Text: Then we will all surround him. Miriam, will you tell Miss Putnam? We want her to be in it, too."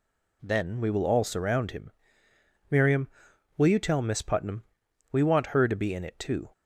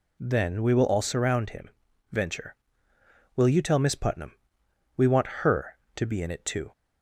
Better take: first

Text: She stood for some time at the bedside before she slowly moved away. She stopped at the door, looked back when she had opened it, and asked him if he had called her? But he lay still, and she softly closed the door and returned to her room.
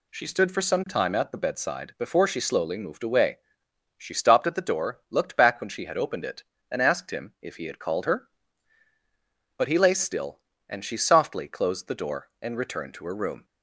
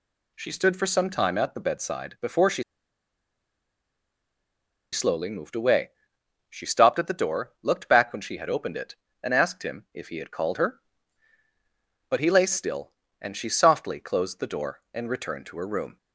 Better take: first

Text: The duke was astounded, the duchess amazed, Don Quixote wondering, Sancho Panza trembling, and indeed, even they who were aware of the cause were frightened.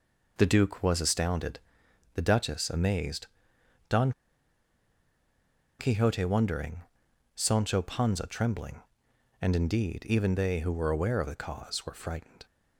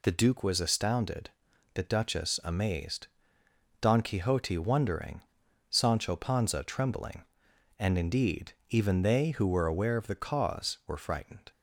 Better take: second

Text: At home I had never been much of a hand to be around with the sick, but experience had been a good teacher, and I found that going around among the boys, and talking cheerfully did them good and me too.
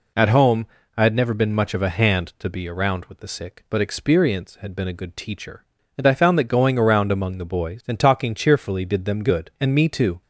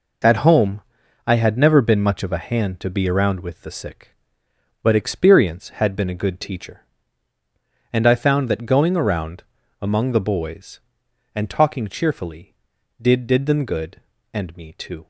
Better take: first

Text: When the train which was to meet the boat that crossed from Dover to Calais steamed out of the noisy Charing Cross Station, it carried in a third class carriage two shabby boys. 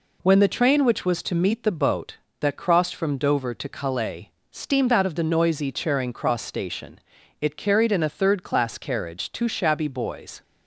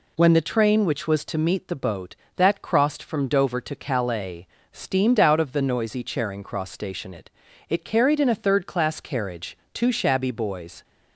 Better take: first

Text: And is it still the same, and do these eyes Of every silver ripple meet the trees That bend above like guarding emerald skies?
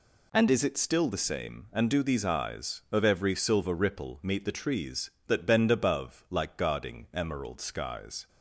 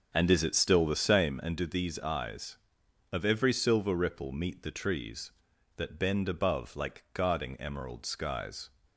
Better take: first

